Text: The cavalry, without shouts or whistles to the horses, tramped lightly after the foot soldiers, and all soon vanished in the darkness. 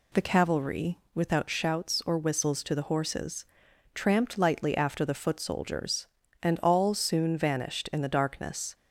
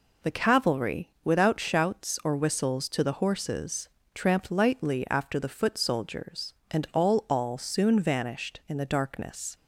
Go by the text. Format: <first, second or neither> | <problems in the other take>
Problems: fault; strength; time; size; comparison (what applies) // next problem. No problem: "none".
first | says "all" twice; at 7.2 s